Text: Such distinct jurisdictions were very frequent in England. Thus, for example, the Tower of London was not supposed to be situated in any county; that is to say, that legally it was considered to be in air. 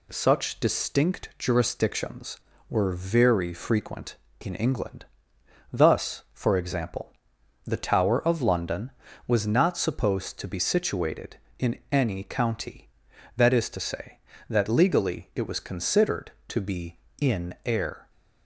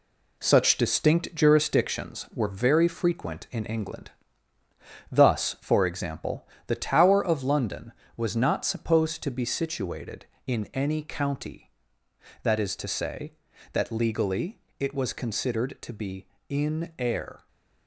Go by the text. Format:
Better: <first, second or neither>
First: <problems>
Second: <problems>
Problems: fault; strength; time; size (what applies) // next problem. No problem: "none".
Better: first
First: none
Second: gets quieter; throughout; 6 dB // pauses between "legally" and "it"; slight; at 14.5 s; 0.20 s long